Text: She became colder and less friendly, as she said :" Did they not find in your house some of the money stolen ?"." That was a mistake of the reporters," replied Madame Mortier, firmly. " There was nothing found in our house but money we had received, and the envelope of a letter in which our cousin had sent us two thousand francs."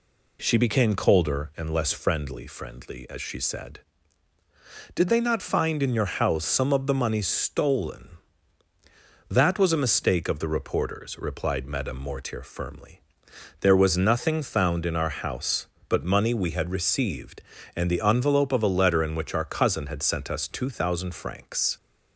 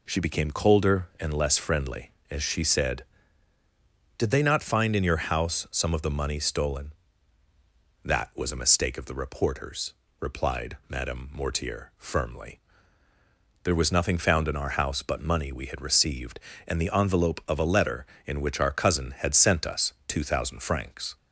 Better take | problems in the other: second | says "friendly" twice; at 2.4 s

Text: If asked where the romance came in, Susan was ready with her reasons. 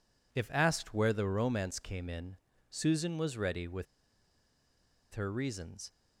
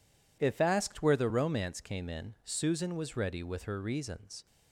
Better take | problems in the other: second | pauses between "with" and "her"; strong; at 3.8 s; 1.2 s long

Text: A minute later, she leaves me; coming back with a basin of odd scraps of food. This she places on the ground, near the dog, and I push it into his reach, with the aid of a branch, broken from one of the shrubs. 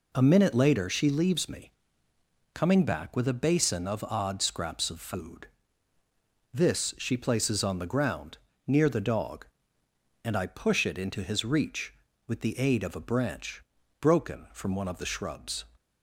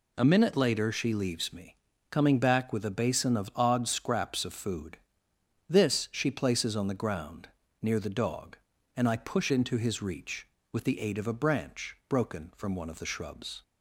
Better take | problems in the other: first | skips "it"; at 9.5 s

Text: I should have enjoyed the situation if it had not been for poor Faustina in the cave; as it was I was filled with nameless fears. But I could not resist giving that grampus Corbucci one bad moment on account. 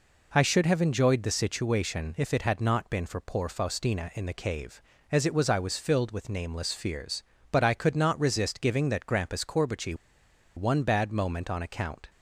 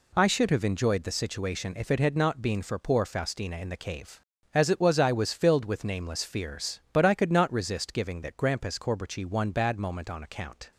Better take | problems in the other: second | pauses between "Corbucci" and "one"; noticeable; at 9.9 s; 0.62 s long

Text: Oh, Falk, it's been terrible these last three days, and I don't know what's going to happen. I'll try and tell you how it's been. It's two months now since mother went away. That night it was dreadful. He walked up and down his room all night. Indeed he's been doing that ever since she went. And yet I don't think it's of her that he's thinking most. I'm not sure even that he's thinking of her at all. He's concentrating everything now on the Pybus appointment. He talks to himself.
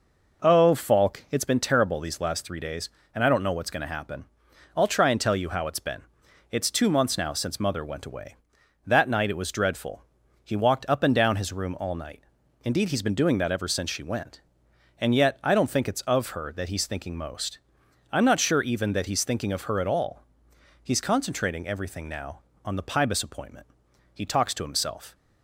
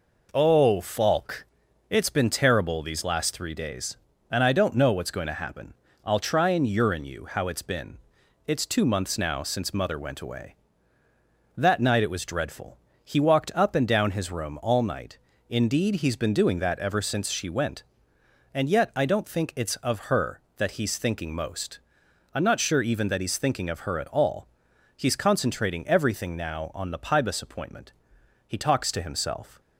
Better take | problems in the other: first | says "urine" for "tell"; at 6.6 s

